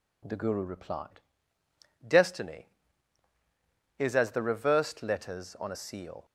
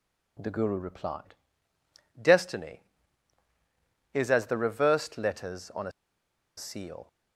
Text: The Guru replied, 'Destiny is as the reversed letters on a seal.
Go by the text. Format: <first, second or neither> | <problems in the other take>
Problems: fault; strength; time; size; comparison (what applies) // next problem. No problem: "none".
first | pauses between "a" and "seal"; noticeable; at 5.9 s; 0.65 s long